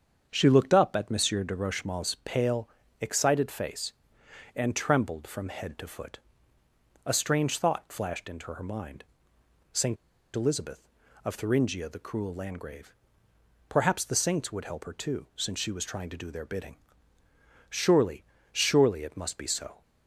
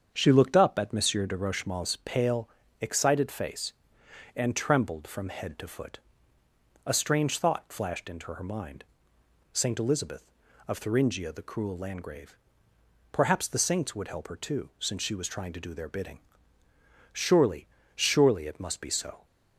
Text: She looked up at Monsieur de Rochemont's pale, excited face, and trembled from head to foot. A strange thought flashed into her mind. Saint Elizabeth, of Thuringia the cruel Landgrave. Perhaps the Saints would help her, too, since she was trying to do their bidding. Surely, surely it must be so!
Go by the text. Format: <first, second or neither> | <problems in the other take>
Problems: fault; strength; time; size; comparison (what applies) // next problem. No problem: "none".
second | starts louder than the rest; strong; until 1.3 s; 7 dB; strong in the second // pauses between "Saint" and "Elizabeth"; at 9.9 s; 0.37 s long